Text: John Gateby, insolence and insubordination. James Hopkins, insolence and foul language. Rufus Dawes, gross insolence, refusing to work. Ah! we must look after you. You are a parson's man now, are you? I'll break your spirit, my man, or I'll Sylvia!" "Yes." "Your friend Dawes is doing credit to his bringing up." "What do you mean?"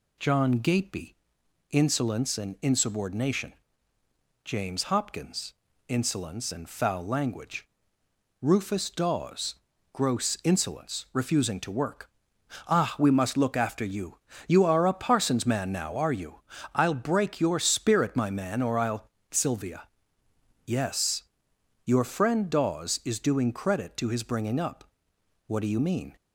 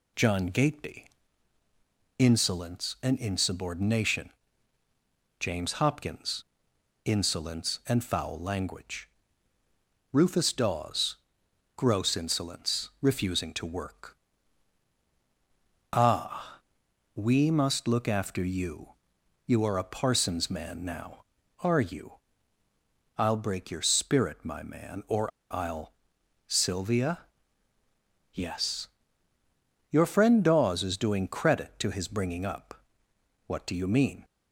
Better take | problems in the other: first | pauses between "or" and "I'll"; slight; at 25.3 s; 0.24 s long // pauses between "I'll" and "Sylvia"; noticeable; at 25.9 s; 0.54 s long; slight in the first

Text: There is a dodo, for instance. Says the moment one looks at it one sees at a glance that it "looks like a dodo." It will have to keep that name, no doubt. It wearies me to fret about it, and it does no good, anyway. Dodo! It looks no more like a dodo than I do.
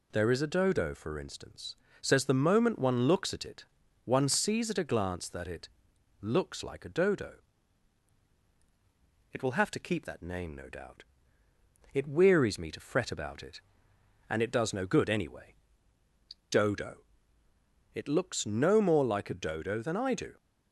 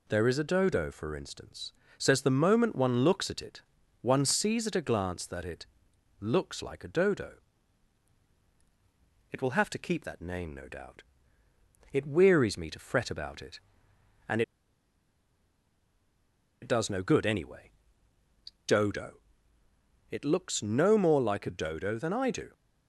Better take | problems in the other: first | pauses between "it" and "one"; at 3.6 s; 0.40 s long; also in the first // pauses between "it" and "looks"; noticeable; at 5.6 s; 0.54 s long; noticeable in the first // pauses between "and" and "it"; strong; at 14.4 s; 2.2 s long

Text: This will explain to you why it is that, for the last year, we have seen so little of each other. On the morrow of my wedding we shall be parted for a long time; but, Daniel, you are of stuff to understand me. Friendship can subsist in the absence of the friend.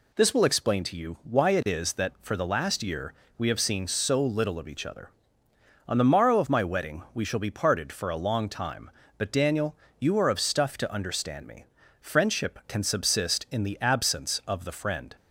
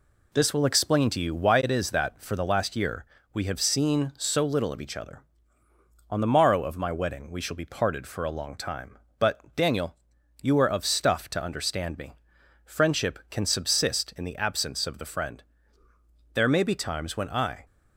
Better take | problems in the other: first | goes on to say "There may be times when I"; noticeable; from 16.3 s on; 1.2 s long

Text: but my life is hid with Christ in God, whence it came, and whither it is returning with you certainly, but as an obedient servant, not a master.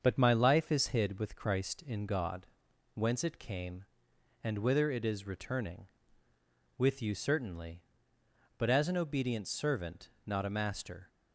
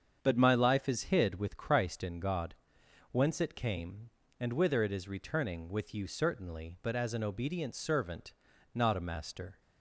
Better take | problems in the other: neither | starts louder than the rest; the same in both

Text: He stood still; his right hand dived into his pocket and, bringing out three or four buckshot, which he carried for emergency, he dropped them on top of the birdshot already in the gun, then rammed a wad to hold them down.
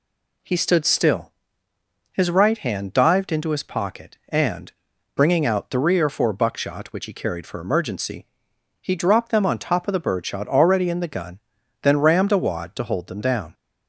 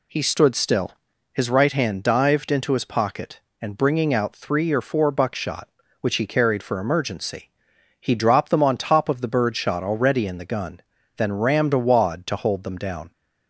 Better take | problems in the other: neither | none

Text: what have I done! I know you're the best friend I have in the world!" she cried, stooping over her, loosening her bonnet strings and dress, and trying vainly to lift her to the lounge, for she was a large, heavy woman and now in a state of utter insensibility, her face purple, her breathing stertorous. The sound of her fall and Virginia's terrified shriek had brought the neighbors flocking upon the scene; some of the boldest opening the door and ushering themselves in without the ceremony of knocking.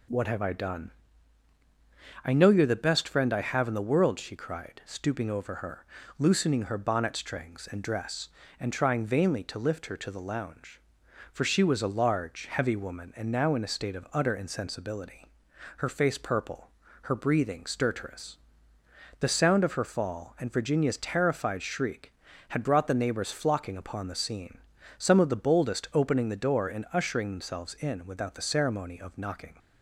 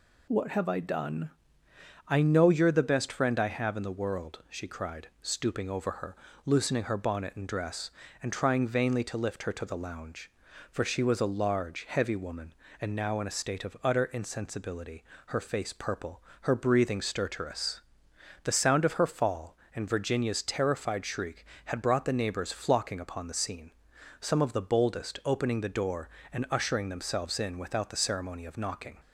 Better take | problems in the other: first | skips "strings"; at 7.3 s

